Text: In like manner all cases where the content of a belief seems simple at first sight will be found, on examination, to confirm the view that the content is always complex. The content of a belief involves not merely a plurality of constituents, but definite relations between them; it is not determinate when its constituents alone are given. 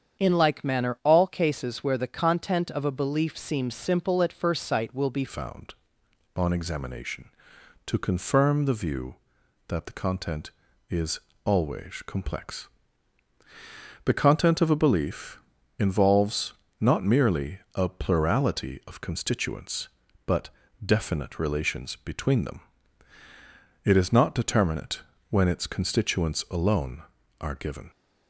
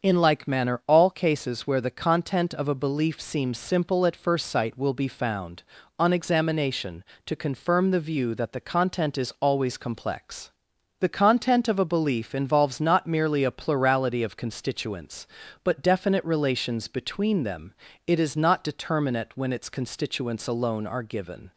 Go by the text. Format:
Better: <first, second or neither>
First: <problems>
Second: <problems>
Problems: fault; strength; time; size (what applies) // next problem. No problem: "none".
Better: second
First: starts louder than the rest; strong; until 1.2 s; 8 dB // changes voice at "found"; from 5.2 s on; 22.6 s long // pauses between "is" and "always"; slight; at 11.1 s; 0.24 s long // pauses between "belief" and "involves"; at 15.3 s; 0.40 s long // pauses between "involves" and "not"; slight; at 16.5 s; 0.26 s long // pauses between "merely" and "a"; slight; at 17.5 s; 0.16 s long // pauses between "but" and "definite"; slight; at 20.4 s; 0.36 s long // pauses between "determinate" and "when"; slight; at 25.0 s; 0.28 s long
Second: starts louder than the rest; until 1.0 s; 7 dB